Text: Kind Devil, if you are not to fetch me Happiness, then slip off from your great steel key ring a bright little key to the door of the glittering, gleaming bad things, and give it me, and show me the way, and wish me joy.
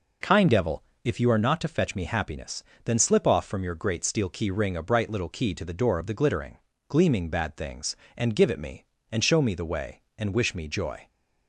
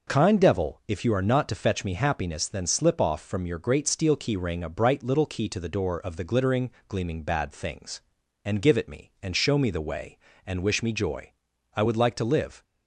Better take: first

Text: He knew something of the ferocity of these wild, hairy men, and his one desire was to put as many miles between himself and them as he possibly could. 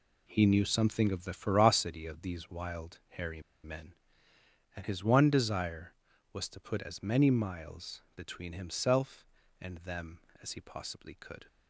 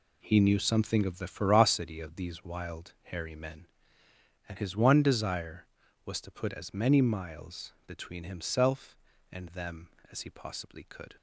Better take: second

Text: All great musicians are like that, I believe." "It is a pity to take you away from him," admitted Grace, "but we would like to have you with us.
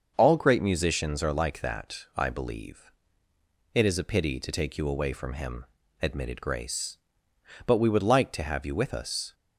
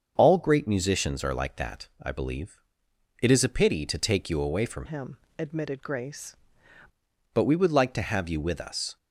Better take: first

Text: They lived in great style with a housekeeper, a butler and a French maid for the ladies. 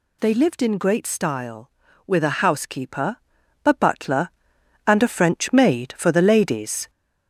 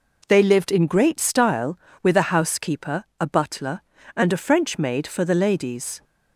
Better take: second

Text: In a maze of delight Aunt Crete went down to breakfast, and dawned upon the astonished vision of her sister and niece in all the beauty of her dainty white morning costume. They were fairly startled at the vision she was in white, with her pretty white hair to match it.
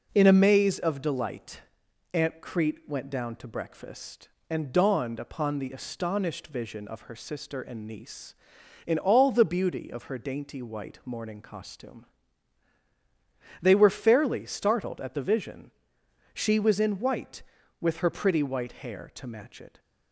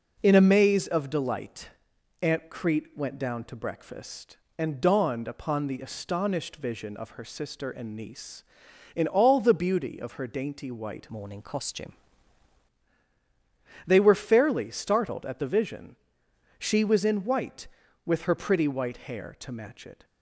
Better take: first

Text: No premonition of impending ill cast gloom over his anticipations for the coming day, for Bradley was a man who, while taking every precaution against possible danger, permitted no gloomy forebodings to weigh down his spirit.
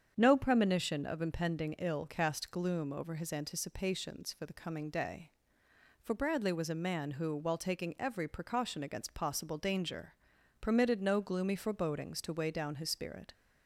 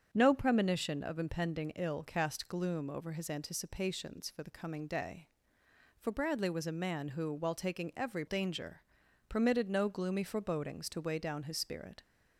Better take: first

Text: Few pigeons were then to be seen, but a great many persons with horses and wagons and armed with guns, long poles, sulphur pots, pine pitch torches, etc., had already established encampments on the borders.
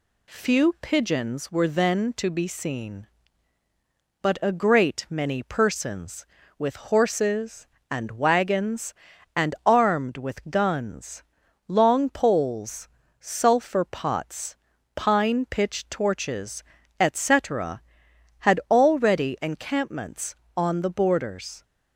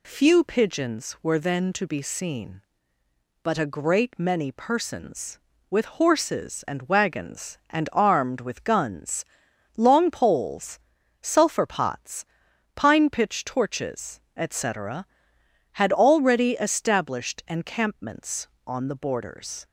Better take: second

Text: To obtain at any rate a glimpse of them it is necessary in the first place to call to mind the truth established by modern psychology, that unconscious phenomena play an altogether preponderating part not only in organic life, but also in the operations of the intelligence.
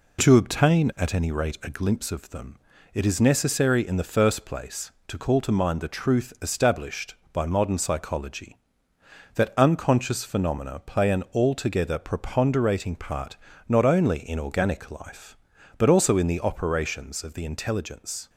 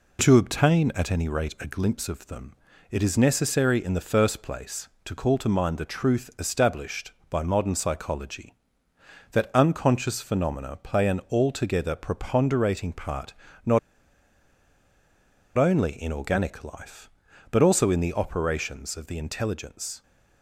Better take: first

